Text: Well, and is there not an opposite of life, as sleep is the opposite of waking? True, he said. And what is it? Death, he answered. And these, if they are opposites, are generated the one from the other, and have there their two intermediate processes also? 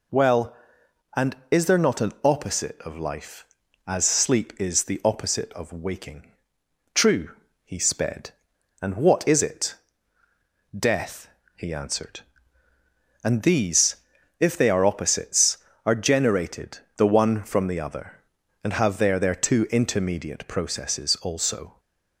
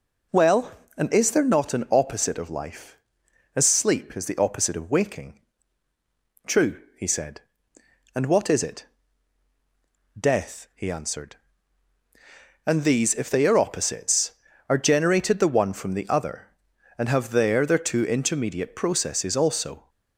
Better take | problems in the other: second | says "sped" for "said"; at 7.7 s // pauses between "generated" and "the"; slight; at 16.7 s; 0.18 s long

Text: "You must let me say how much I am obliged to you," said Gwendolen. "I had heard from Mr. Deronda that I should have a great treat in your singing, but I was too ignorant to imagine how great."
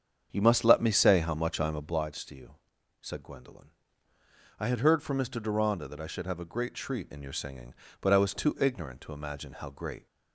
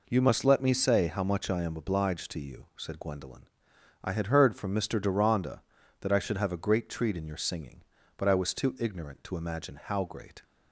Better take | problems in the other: second | starts louder than the rest; strong; until 2.1 s; 7.5 dB

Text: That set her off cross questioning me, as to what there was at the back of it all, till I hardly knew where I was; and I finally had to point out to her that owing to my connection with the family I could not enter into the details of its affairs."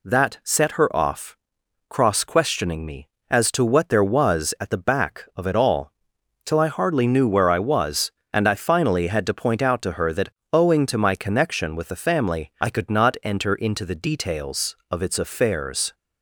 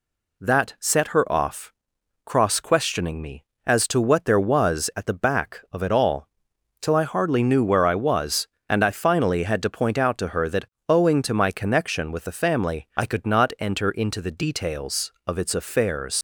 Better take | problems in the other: first | pauses between "off" and "cross"; noticeable; at 1.7 s; 0.54 s long; noticeable in the first // pauses between "that" and "owing"; slight; at 10.6 s; 0.24 s long; slight in the first // leaves "affairs" unfinished; at 16.1 s; 90 ms

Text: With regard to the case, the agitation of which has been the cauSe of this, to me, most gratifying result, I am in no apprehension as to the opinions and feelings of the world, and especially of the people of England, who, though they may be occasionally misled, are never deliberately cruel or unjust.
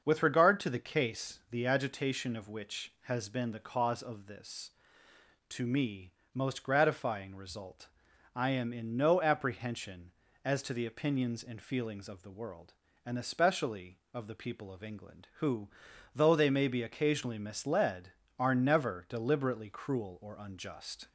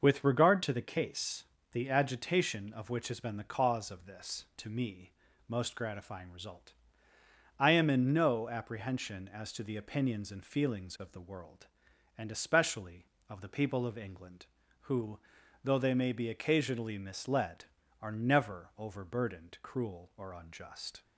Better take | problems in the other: first | starts louder than the rest; noticeable; until 1.0 s; 6 dB; also in the first // says "overburdened" for "deliberately"; at 18.7 s

